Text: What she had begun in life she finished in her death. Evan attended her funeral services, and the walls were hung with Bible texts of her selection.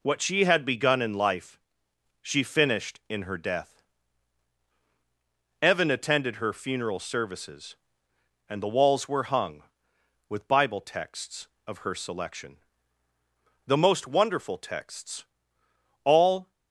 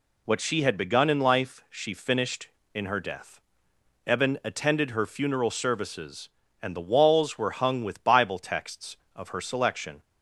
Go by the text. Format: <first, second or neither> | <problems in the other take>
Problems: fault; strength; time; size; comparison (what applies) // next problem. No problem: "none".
second | pauses between "life" and "she"; noticeable; at 1.5 s; 0.64 s long // goes on to say "The most wonderful texts All"; strong; from 13.6 s on; 2.8 s long